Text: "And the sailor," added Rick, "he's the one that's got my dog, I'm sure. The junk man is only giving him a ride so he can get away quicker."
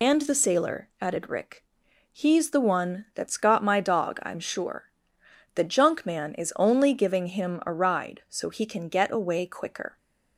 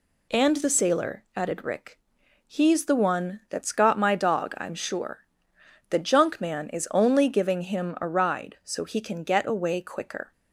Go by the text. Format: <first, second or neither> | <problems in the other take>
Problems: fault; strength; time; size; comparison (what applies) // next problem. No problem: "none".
second | loses the start of "And"; at 0.0 s; 60 ms